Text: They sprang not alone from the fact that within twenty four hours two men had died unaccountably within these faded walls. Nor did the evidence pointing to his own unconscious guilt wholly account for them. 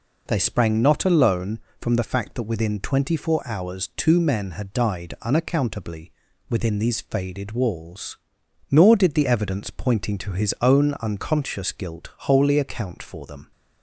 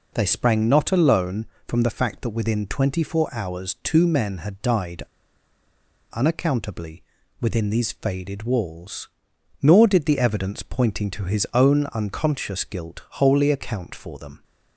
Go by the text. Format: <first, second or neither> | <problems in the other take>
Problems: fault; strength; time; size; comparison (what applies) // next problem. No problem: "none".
first | pauses between "died" and "unaccountably"; at 5.0 s; 1.0 s long // pauses between "unaccountably" and "within"; slight; at 7.0 s; 0.36 s long; slight in the first